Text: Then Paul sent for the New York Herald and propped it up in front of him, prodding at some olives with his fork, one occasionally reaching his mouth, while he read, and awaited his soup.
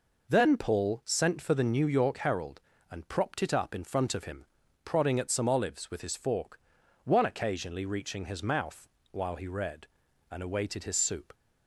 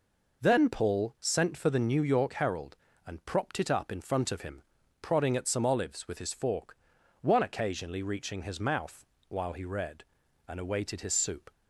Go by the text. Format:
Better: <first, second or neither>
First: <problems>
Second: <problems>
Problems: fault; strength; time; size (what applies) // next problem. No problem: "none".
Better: neither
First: none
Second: none